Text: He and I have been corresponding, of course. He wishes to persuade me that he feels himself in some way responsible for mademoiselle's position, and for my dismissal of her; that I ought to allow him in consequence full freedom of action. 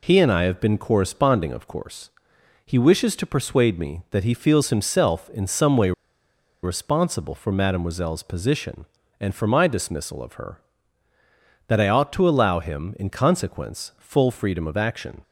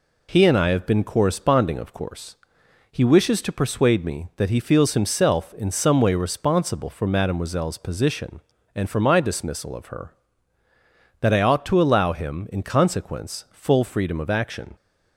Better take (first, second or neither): second